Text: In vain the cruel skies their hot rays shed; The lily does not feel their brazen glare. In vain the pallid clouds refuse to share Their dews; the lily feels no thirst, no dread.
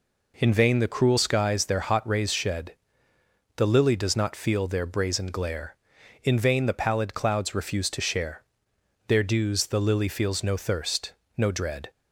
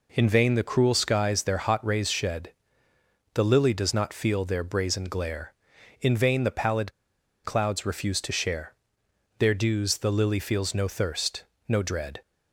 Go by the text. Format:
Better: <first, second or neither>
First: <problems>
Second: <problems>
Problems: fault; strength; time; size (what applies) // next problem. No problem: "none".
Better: first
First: pauses between "share" and "Their"; noticeable; at 8.4 s; 0.66 s long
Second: pauses between "pallid" and "clouds"; noticeable; at 6.9 s; 0.53 s long // pauses between "share" and "Their"; noticeable; at 8.7 s; 0.66 s long